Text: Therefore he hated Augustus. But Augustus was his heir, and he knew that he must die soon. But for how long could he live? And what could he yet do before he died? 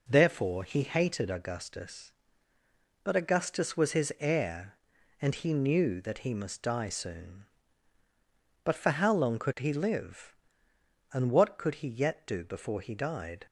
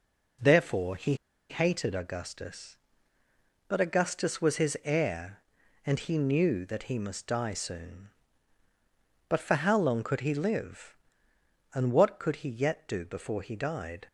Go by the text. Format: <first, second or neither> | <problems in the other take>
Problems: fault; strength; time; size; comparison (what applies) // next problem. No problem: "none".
first | pauses between "he" and "hated"; slight; at 1.1 s; 0.35 s long